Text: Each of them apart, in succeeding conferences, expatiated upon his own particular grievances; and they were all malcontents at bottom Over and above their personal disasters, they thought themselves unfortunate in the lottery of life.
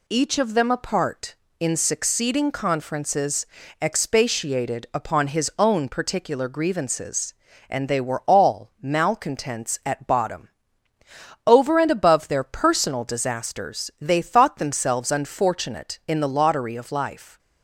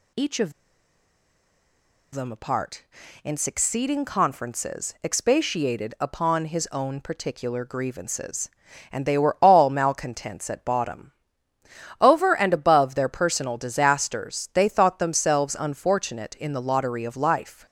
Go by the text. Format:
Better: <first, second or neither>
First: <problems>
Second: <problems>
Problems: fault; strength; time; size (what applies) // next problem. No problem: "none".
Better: first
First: pauses between "bottom" and "Over"; noticeable; at 10.4 s; 0.96 s long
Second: pauses between "of" and "them"; strong; at 0.5 s; 1.6 s long // pauses between "bottom" and "Over"; noticeable; at 11.1 s; 0.86 s long